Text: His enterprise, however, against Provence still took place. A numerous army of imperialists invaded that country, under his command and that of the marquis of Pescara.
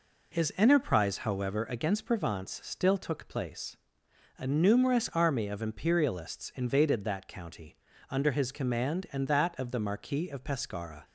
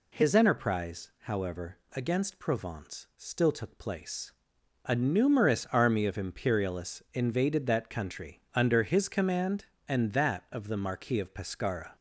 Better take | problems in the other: second | says "county" for "country"; at 7.2 s

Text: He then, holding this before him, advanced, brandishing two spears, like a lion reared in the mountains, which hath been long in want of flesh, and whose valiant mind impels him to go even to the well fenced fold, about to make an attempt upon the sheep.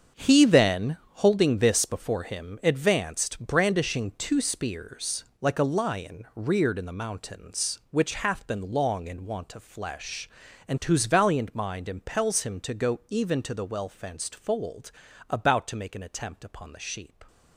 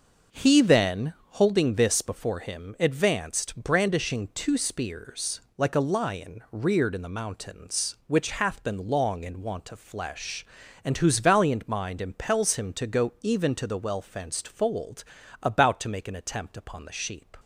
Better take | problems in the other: second | gets quieter; strong; throughout; 11 dB // starts louder than the rest; strong; until 1.3 s; 7.5 dB; also in the second

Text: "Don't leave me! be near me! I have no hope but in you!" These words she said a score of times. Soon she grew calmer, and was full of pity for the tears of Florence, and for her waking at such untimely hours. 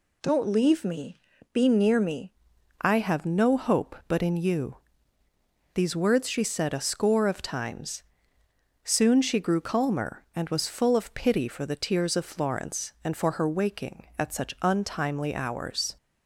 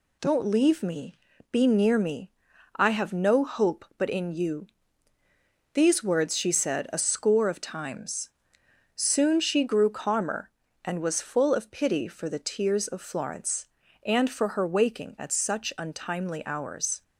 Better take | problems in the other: second | changes voice at "I"; from 2.8 s on; 13.1 s long

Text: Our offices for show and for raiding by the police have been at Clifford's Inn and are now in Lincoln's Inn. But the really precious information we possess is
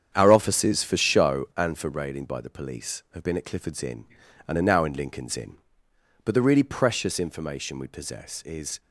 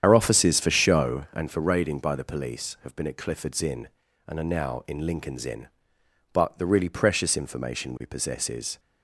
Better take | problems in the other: first | loses the start of "Our"; at 0.0 s; 75 ms // starts louder than the rest; strong; until 1.0 s; 9 dB; strong in the first

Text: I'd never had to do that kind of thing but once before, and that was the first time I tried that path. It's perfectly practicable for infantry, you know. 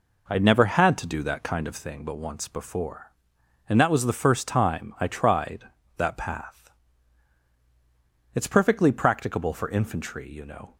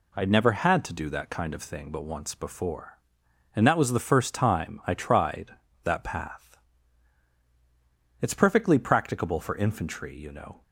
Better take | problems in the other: second | starts louder than the rest; noticeable; until 1.9 s; 4.5 dB

